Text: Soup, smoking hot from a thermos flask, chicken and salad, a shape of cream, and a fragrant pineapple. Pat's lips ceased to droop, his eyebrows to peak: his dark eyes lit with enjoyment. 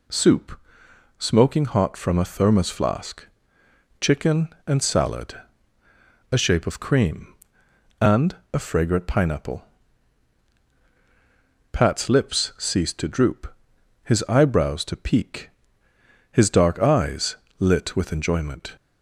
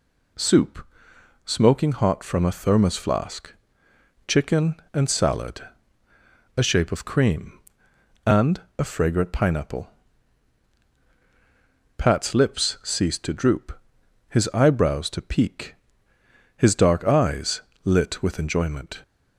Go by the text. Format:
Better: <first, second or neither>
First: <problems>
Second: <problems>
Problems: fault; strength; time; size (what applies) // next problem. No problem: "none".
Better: neither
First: pauses between "and" and "a"; slight; at 8.3 s; 0.18 s long // pauses between "eyes" and "lit"; slight; at 17.3 s; 0.24 s long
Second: pauses between "and" and "a"; slight; at 8.6 s; 0.18 s long // pauses between "eyes" and "lit"; slight; at 17.6 s; 0.24 s long